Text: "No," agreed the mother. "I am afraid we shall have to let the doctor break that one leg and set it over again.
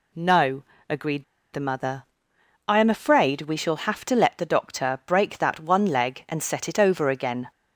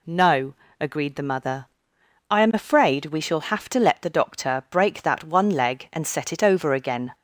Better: second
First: pauses between "agreed" and "the"; slight; at 1.2 s; 0.28 s long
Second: none

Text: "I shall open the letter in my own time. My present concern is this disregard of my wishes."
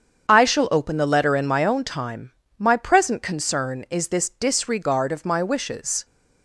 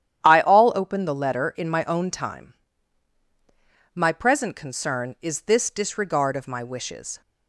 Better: first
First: starts louder than the rest; strong; until 1.3 s; 8 dB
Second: starts louder than the rest; strong; until 1.2 s; 10.5 dB // says "all" for "shall"; at 0.4 s

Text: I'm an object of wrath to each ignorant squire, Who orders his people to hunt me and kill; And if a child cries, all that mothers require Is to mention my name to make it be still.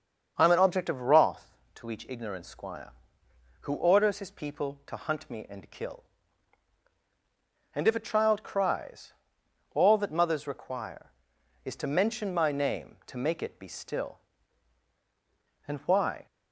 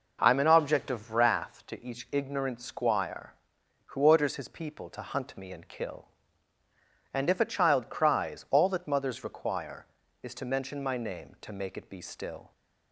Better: second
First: starts louder than the rest; until 1.3 s; 7 dB // goes on to say "And why"; from 15.6 s on; 0.60 s long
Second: none

